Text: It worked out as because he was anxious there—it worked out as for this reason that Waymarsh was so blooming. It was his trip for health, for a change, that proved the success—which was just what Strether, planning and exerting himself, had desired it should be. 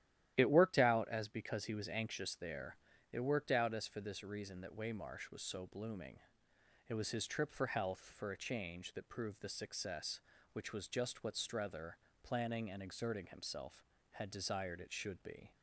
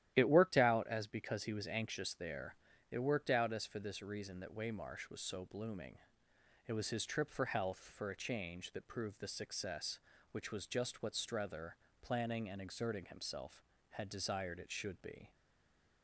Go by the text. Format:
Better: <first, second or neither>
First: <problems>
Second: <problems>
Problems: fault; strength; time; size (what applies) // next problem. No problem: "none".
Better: first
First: starts louder than the rest; strong; until 1.3 s; 12 dB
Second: starts louder than the rest; strong; until 1.1 s; 12 dB // stays silent after the last word; slight; from 15.3 s on; 0.7 s long